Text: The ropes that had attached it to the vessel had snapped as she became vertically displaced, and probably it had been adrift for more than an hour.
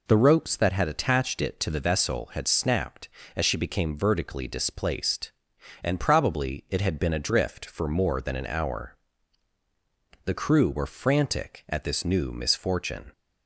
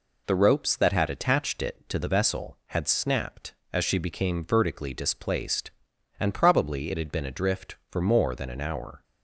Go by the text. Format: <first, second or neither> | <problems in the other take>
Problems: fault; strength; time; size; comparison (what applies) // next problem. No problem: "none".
second | goes on to say "The crew were frantic at this new misfortune"; strong; from 10.2 s on; 2.8 s long